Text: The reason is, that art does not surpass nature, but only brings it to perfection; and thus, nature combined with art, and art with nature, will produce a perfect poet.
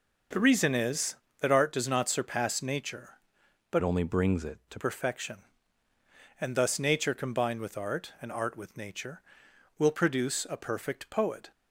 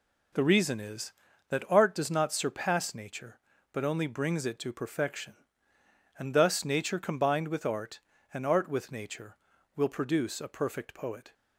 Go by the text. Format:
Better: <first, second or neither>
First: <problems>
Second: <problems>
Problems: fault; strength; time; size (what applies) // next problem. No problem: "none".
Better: second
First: changes voice from "only" to "to"; from 3.8 to 4.7 s; 0.9 s long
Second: none